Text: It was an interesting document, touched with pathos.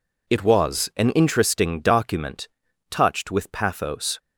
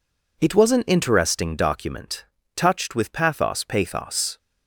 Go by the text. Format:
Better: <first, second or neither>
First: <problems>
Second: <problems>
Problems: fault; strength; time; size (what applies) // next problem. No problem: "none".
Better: first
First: none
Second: says "pathos" twice; at 3.6 s